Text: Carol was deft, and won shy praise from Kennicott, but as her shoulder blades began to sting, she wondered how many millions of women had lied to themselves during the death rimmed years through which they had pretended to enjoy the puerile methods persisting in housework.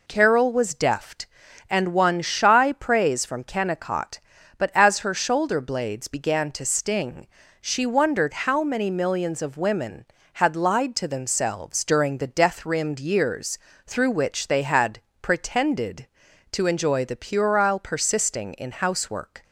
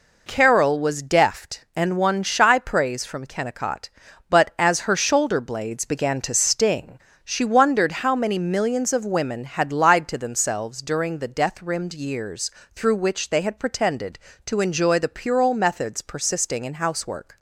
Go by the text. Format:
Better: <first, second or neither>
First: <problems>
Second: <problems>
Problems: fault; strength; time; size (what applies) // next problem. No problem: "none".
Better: second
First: pauses between "years" and "through"; slight; at 13.5 s; 0.28 s long // pauses between "had" and "pretended"; slight; at 15.0 s; 0.20 s long // skips "methods"; at 17.7 s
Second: pauses between "years" and "through"; slight; at 12.5 s; 0.24 s long